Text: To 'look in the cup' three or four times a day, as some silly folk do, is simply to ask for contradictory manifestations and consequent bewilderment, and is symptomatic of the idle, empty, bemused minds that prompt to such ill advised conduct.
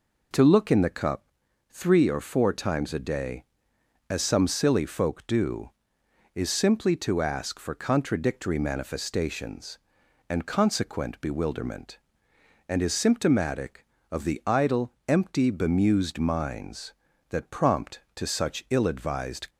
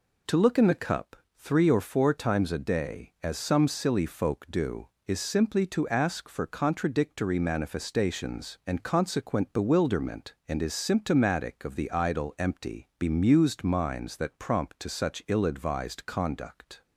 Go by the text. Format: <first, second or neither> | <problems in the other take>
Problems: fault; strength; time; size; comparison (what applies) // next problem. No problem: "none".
second | pauses between "cup" and "three"; at 1.2 s; 0.44 s long; slight in the second // stops before "conduct"; at 19.4 s